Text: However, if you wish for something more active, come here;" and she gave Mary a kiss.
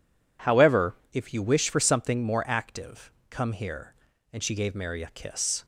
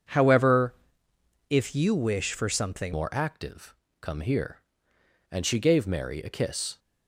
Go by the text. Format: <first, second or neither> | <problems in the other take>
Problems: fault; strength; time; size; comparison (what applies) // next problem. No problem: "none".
first | changes voice at "more"; from 2.9 s on; 3.8 s long